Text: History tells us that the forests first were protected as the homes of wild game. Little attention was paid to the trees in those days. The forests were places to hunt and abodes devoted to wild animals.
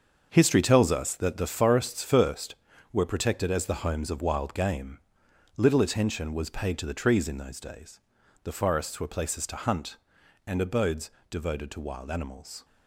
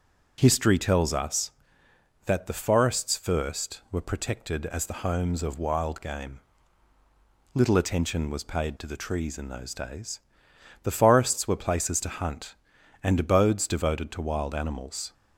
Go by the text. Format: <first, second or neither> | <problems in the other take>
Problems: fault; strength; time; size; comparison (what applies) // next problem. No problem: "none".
second | gets quieter; strong; throughout; 10 dB // starts louder than the rest; until 1.3 s; 6.5 dB; also in the second // pauses between "abodes" and "devoted"; slight; at 11.0 s; 0.22 s long